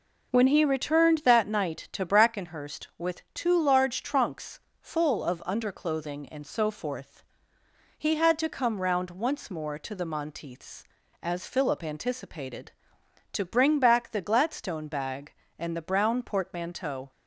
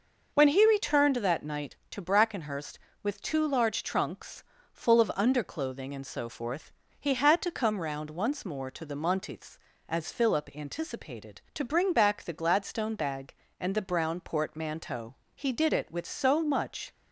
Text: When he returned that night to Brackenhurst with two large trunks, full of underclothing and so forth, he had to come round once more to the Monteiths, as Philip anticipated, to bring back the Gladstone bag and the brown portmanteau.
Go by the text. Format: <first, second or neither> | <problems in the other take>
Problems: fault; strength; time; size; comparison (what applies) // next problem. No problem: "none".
first | goes on to say "He did it with so much"; from 15.3 s on; 1.5 s long